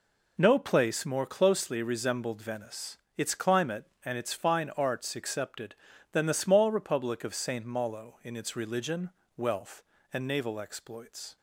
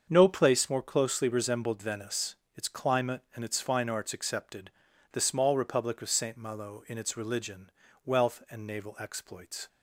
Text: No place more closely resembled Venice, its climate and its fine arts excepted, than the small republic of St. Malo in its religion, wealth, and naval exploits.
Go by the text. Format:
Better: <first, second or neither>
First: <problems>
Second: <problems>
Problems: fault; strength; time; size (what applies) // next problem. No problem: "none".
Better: first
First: none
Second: starts louder than the rest; until 1.1 s; 7 dB // skips "than"; at 4.9 s